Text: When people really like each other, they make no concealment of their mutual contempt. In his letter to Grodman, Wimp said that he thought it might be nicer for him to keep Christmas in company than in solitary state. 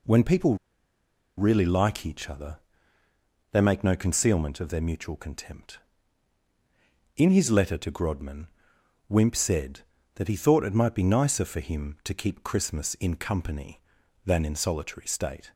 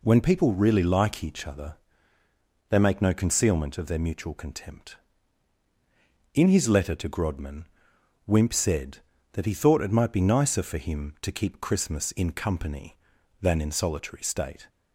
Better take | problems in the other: second | pauses between "people" and "really"; noticeable; at 0.5 s; 0.81 s long

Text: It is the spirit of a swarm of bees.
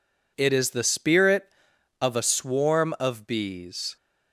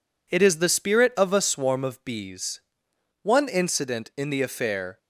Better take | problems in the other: first | goes on to say "One incident in the affair"; strong; from 3.2 s on; 1.7 s long

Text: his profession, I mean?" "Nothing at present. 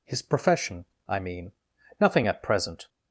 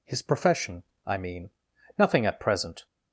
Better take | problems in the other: neither | none

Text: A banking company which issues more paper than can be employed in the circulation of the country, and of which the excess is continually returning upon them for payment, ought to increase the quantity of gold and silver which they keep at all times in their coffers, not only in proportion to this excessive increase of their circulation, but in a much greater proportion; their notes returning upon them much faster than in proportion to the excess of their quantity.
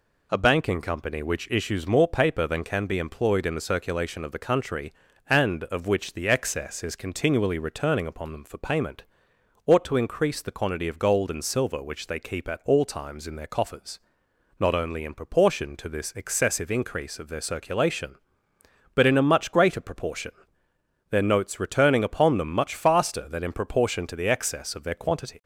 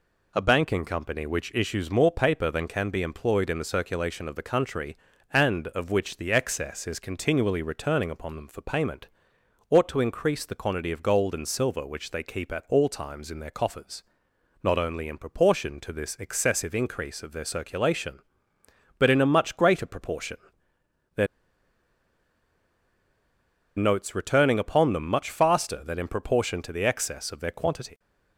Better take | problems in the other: first | pauses between "their" and "notes"; strong; at 21.2 s; 2.5 s long

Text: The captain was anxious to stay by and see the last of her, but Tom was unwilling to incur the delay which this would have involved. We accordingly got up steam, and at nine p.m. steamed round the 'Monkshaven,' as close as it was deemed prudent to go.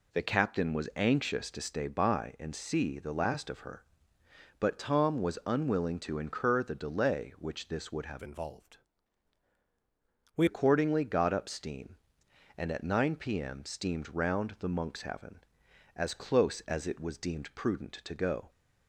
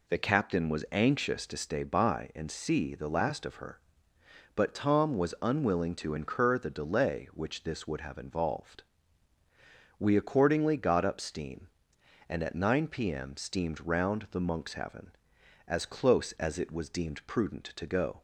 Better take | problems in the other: second | changes voice from "involved" to "We"; from 8.2 to 10.4 s; 2.2 s long

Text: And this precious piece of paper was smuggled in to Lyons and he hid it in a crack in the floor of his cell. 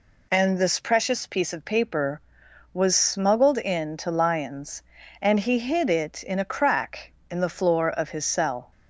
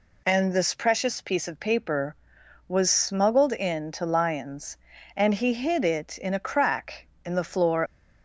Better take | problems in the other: first | stops before "of his cell"; at 7.8 s

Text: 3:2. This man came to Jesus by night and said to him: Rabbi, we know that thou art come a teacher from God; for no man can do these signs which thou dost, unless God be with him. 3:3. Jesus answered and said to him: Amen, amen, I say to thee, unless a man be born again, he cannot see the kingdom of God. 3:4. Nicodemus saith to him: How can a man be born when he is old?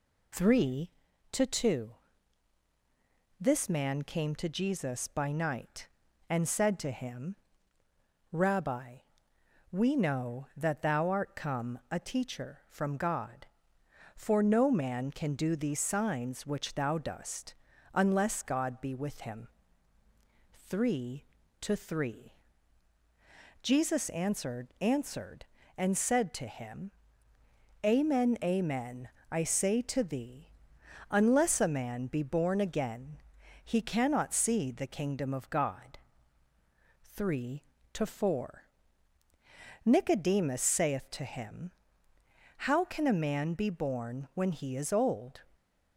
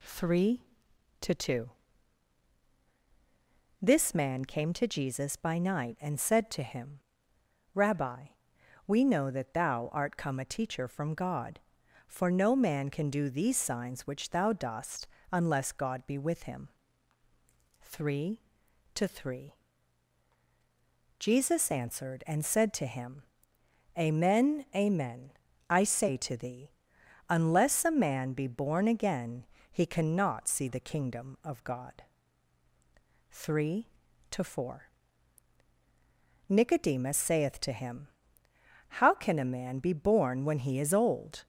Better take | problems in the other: second | says "answered" twice; at 24.8 s

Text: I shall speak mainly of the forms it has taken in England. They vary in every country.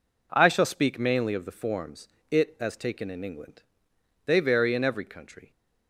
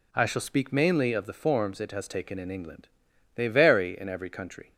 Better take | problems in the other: second | pauses between "forms" and "it"; slight; at 2.0 s; 0.24 s long // says "as" for "has"; at 2.6 s

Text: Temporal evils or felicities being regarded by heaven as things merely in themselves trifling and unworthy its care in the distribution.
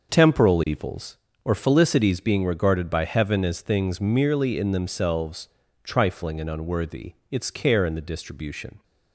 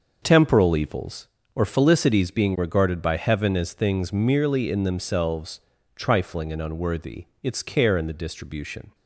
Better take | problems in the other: neither | starts louder than the rest; the same in both // pauses between "themselves" and "trifling"; slight; the same in both // pauses between "unworthy" and "its"; slight; the same in both

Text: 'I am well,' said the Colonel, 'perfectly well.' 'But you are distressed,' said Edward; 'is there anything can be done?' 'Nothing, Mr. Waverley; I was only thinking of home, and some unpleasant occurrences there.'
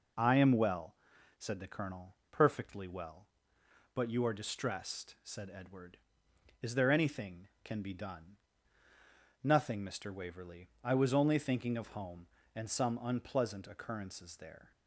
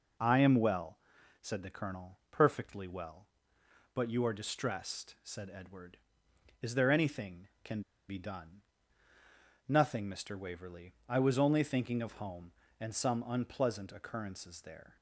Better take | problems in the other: first | pauses between "can" and "be"; slight; at 7.8 s; 0.27 s long

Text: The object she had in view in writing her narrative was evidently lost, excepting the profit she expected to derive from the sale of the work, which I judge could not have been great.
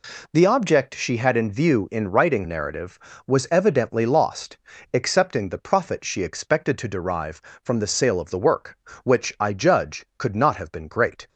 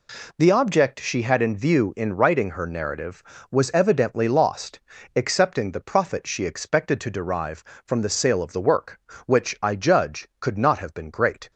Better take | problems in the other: second | skips "her"; at 2.4 s

